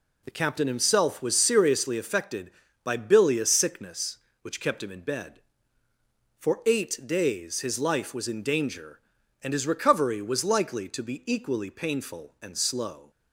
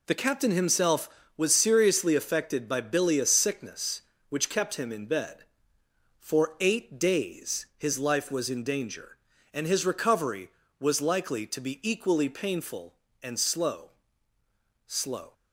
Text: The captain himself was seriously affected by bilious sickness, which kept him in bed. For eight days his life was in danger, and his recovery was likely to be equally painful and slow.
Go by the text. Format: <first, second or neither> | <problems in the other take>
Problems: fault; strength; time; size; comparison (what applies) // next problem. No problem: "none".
first | says "slow" twice; at 14.8 s